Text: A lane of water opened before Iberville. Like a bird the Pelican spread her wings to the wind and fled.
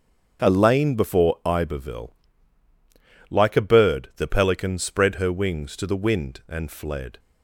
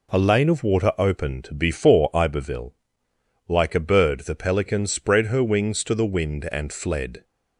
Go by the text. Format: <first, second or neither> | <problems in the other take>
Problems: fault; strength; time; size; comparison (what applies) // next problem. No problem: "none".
second | starts louder than the rest; until 1.5 s; 7 dB // skips "of water opened"; at 0.9 s